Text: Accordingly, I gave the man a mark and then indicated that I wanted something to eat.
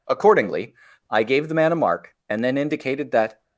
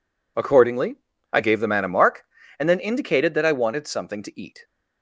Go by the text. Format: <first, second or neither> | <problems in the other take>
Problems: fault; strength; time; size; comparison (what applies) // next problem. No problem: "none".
second | stops before "I wanted something to eat"; at 3.4 s